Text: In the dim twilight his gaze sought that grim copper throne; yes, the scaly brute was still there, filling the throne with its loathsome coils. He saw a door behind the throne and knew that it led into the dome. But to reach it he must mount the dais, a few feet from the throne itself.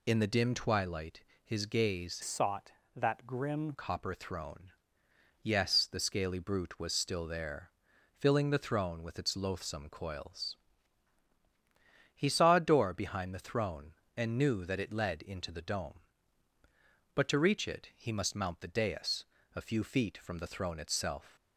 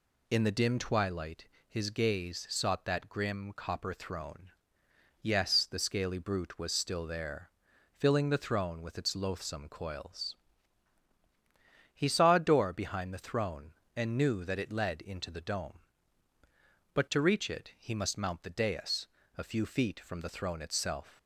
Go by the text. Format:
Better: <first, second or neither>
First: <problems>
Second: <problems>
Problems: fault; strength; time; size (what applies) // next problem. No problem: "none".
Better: second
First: pauses between "twilight" and "his"; slight; at 1.2 s; 0.22 s long // changes voice from "sought" to "grim"; from 2.2 to 3.7 s; 1.5 s long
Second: pauses between "twilight" and "his"; slight; at 1.4 s; 0.22 s long